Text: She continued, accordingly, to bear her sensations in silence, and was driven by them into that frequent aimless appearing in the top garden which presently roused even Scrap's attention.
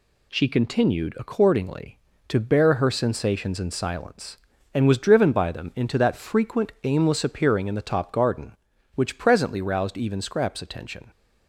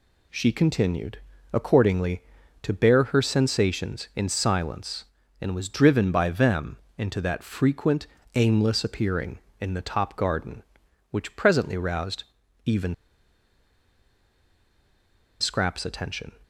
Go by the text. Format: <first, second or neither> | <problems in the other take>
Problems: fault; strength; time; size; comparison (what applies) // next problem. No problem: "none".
first | pauses between "them" and "into"; slight; at 6.7 s; 0.20 s long // pauses between "frequent" and "aimless"; slight; at 8.0 s; 0.30 s long // pauses between "roused" and "even"; at 12.2 s; 0.42 s long // pauses between "even" and "Scrap's"; strong; at 12.9 s; 2.4 s long